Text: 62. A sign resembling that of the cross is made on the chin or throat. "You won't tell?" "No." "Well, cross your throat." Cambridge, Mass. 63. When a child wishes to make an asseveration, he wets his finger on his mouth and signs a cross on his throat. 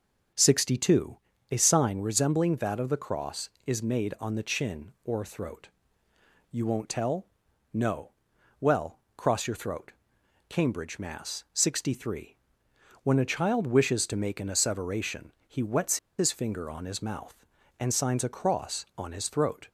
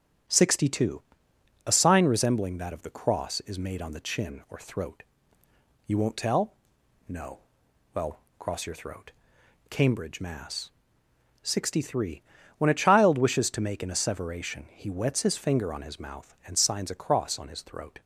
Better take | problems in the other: second | starts louder than the rest; until 1.6 s; 7 dB; strong in the second // pauses between "wets" and "his"; slight; at 15.9 s; 0.21 s long

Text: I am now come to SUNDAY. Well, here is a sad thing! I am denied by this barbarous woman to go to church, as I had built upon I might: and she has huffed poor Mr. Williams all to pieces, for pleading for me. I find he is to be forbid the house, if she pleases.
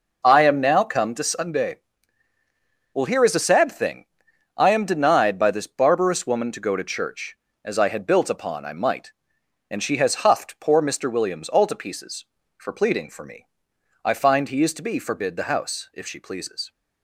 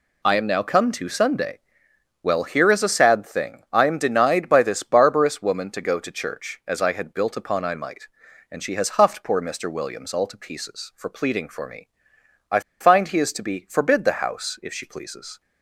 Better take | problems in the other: first | pauses between "I" and "find"; slight; at 12.6 s; 0.20 s long

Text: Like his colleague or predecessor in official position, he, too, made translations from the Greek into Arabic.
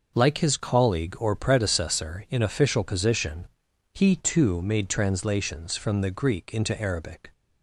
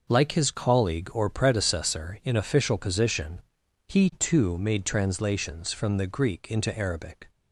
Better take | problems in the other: neither | none

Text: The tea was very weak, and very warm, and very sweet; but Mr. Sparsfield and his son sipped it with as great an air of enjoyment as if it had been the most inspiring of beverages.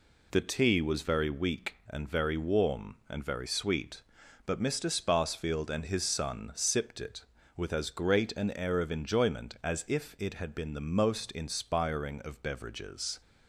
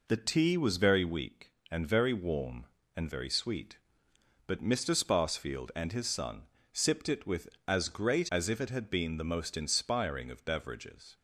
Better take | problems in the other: first | pauses between "son" and "sipped"; slight; at 6.4 s; 0.32 s long // skips "an air of enjoyment"; at 8.2 s

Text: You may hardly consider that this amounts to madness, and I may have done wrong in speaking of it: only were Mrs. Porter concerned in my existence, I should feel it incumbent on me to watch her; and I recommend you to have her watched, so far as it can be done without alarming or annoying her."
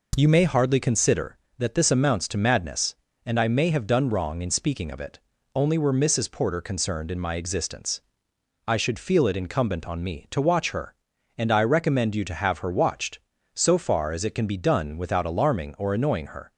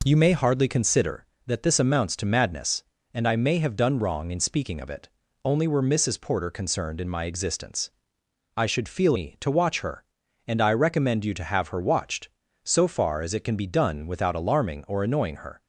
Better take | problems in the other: first | skips "it incumbent on"; at 9.1 s

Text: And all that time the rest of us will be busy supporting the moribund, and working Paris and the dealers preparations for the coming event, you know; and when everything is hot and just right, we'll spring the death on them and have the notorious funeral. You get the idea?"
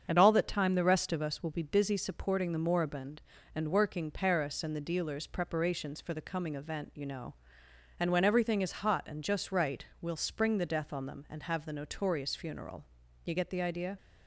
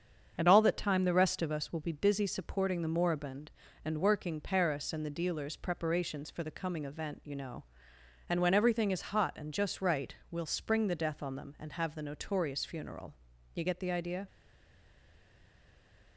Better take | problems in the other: first | starts louder than the rest; strong; until 1.3 s; 7.5 dB; strong in the first // stays silent after the last word; noticeable; from 14.2 s on; 1.9 s long

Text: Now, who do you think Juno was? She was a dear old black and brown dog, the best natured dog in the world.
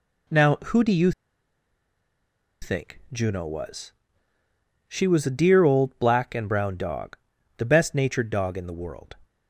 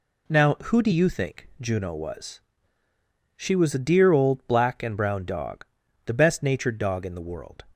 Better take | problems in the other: second | pauses between "you" and "think"; strong; at 1.1 s; 1.5 s long

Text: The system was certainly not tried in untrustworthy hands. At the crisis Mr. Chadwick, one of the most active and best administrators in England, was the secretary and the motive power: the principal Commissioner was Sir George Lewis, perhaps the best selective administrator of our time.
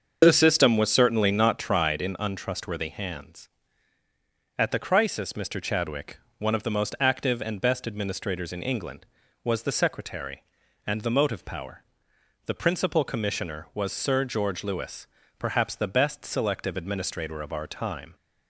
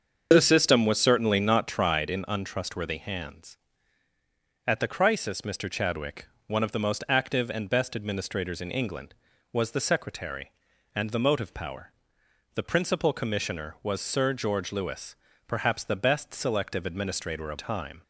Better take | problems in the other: first | starts louder than the rest; until 1.3 s; 6.5 dB; also in the first // skips "our"; at 17.5 s

